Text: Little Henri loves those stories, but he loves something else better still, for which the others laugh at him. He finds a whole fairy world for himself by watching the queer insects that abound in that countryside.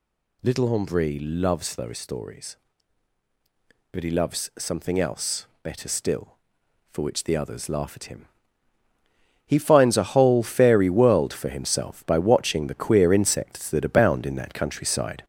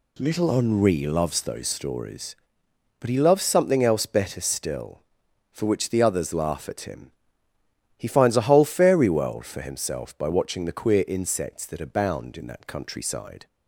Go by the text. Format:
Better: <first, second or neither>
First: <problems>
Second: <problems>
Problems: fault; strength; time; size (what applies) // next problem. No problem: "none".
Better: second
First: gets louder; noticeable; throughout; 5 dB // pauses between "else" and "better"; slight; at 5.4 s; 0.16 s long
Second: none